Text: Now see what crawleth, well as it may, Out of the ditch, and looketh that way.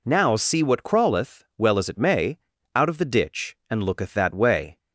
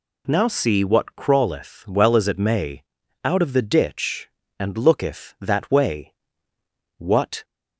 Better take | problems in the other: first | goes on to say "What"; slight; from 6.9 s on; 0.46 s long

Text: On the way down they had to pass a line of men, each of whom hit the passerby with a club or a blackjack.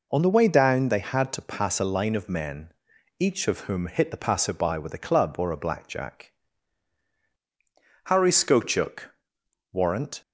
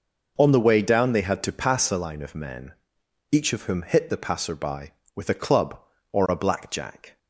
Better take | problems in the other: second | goes on to say "Harry Skochuk Warrant"; strong; from 8.0 s on; 2.1 s long

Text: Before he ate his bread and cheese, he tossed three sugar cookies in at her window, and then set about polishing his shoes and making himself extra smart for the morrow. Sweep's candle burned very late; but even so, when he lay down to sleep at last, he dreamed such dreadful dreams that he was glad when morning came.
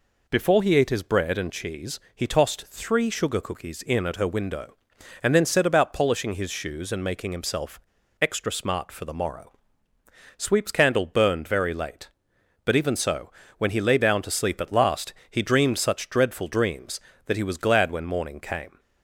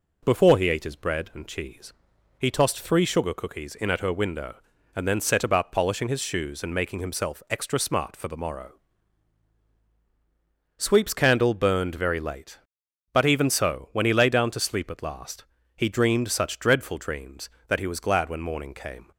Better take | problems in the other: second | pauses between "himself" and "extra"; at 7.7 s; 0.42 s long

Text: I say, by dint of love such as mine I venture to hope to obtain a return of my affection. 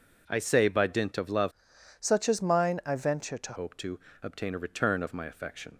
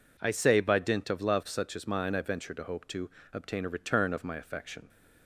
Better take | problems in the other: second | changes voice from "such" to "to"; from 2.0 to 3.5 s; 1.5 s long // pauses between "to" and "obtain"; slight; at 3.9 s; 0.24 s long; slight in the second

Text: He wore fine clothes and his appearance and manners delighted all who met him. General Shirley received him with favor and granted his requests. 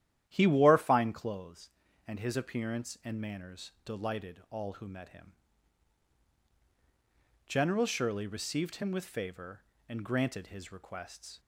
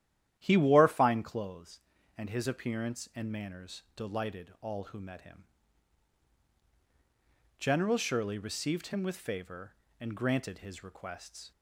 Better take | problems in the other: neither | starts louder than the rest; strong; the same in both

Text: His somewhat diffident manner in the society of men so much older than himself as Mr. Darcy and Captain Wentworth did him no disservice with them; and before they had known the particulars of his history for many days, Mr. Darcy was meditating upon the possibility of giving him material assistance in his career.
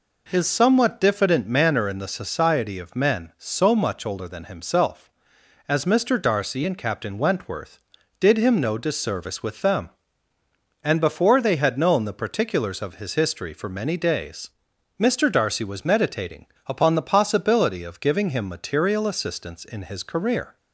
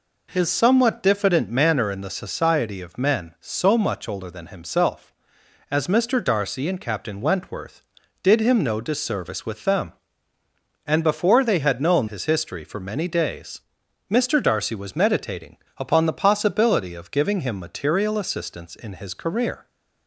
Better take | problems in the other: first | skips "the particulars of"; at 12.0 s // pauses between "meditating" and "upon"; slight; at 15.5 s; 0.20 s long; slight in the first

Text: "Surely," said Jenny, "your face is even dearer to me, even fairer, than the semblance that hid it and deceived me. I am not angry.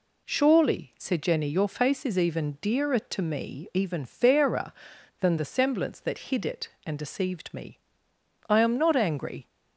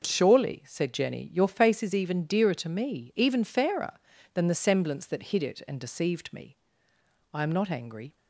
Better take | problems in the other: neither | none

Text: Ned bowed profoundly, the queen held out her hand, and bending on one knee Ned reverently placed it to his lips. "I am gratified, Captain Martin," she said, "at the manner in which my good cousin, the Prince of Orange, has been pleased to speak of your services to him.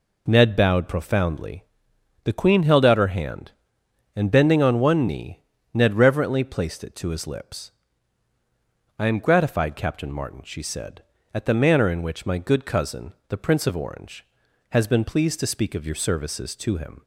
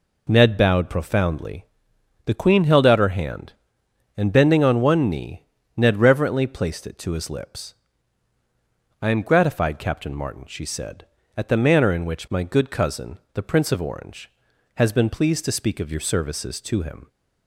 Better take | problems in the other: neither | pauses between "knee" and "Ned"; slight; the same in both

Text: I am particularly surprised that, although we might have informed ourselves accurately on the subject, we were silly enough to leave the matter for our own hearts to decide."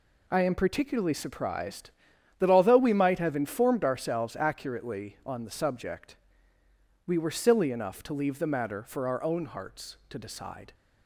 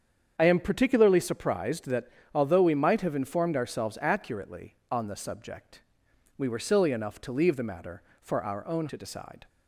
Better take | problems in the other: first | starts louder than the rest; strong; until 1.3 s; 7.5 dB // skips "hearts"; at 8.8 s

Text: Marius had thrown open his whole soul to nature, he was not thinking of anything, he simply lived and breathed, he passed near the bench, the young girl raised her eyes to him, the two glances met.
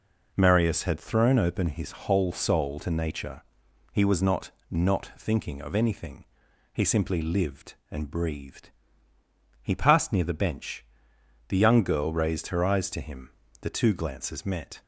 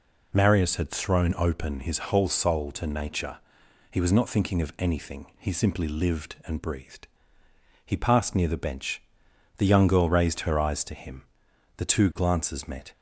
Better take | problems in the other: second | says "not" twice; at 4.6 s

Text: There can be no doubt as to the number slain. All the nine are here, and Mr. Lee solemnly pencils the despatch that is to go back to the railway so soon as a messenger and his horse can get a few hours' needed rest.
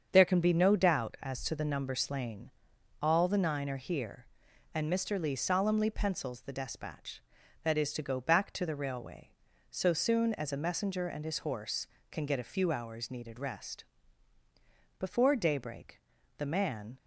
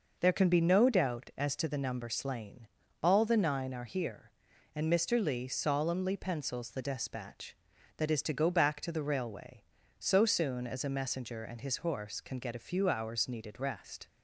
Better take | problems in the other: second | starts louder than the rest; until 1.1 s; 7 dB // goes on to say "Before daybreak the man"; strong; from 14.9 s on; 2.0 s long

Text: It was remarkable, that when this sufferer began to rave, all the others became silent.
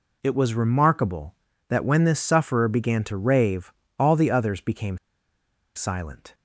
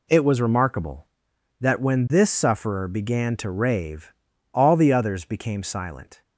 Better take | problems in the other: second | pauses between "became" and "silent"; noticeable; at 4.9 s; 0.77 s long

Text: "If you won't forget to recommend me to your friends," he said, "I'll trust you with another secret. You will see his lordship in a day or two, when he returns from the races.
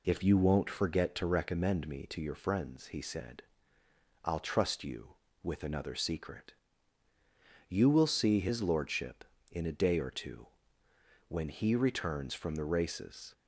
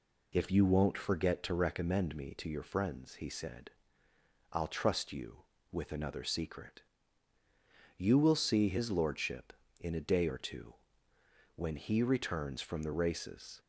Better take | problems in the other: neither | none

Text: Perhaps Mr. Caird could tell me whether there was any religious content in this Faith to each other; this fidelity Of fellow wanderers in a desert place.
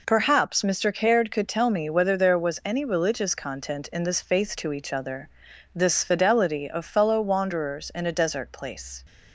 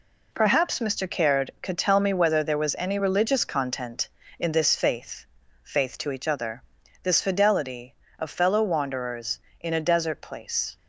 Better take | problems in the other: first | says "Faith" twice; at 5.6 s

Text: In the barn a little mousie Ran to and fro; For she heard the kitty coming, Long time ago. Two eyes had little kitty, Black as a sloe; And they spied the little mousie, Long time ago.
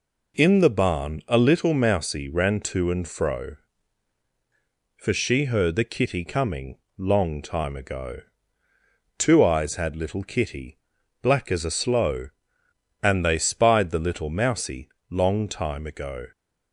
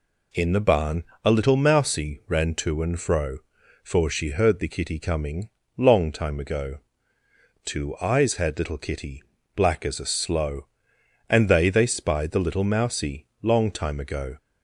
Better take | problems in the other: first | pauses between "barn" and "a"; slight; at 1.0 s; 0.22 s long // says "they" twice; at 11.6 s

